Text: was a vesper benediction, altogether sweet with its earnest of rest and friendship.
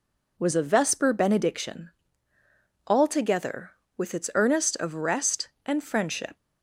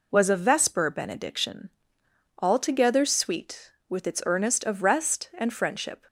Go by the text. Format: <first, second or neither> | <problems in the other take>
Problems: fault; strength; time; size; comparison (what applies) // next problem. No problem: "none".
second | skips "sweet"; at 3.8 s